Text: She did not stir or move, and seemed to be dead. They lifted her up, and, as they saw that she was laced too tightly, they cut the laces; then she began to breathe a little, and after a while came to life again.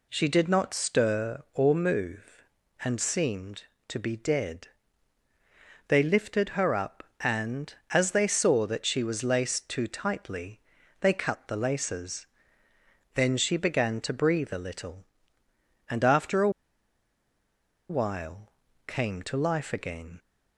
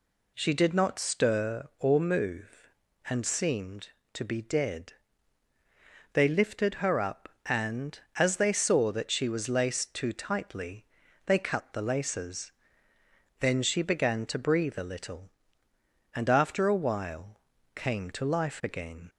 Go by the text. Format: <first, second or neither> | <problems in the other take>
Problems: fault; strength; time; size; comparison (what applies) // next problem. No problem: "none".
second | pauses between "a" and "while"; strong; at 16.4 s; 1.4 s long // pauses between "while" and "came"; slight; at 18.5 s; 0.36 s long; slight in the second